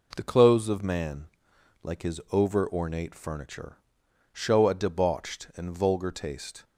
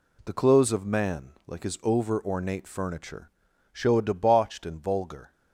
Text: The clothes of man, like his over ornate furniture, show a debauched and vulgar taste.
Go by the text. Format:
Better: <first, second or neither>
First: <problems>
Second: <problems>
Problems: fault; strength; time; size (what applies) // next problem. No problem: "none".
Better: first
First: none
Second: stops before "taste"; at 5.3 s